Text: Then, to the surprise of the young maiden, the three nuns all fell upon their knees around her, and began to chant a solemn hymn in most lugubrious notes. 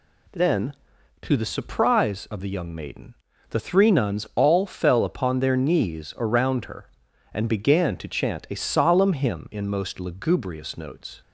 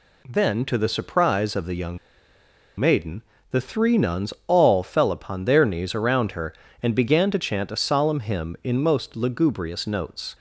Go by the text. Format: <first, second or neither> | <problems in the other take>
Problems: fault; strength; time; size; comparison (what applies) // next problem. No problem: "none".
first | pauses between "young" and "maiden"; noticeable; at 1.9 s; 0.80 s long // pauses between "nuns" and "all"; slight; at 4.3 s; 0.16 s long